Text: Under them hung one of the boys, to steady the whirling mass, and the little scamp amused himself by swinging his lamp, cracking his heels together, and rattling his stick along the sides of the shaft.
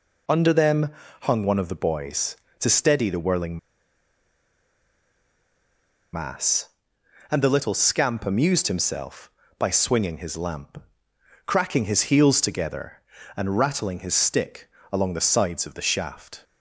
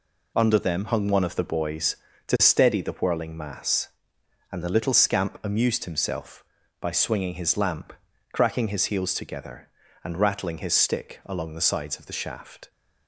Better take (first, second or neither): second